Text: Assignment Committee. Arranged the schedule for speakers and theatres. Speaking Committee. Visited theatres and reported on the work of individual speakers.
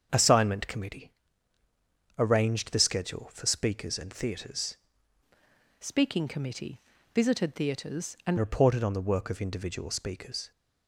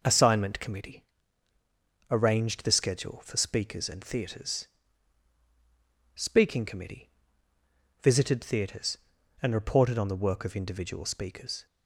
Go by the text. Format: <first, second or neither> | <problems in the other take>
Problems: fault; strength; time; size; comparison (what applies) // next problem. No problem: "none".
second | starts louder than the rest; until 1.1 s; 7 dB // changes voice from "Speaking" to "and"; from 5.7 to 8.3 s; 2.6 s long